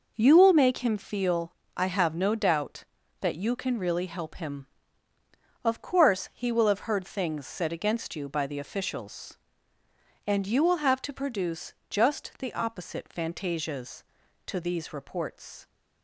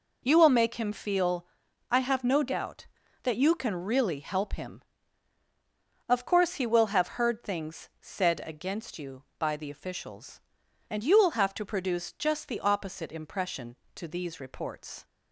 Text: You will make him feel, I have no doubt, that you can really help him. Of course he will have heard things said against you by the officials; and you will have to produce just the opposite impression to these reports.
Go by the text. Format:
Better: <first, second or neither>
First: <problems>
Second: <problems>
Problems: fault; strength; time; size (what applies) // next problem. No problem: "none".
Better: second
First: pauses between "produce" and "just"; slight; at 11.7 s; 0.16 s long // says "fantasias" for "impression"; at 13.1 s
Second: none